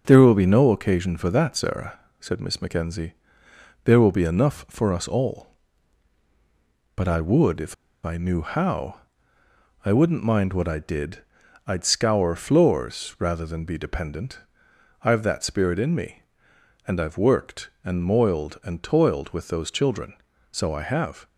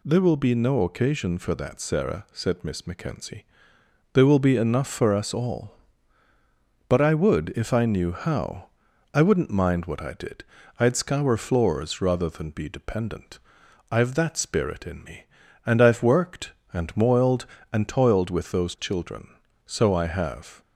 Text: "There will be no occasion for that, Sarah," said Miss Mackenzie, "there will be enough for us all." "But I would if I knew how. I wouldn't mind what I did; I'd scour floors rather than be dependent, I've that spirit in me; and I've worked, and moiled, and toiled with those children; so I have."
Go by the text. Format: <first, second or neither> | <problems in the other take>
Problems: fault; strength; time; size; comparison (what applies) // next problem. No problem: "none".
second | starts louder than the rest; until 1.0 s; 6.5 dB // pauses between "if" and "I"; slight; at 7.7 s; 0.30 s long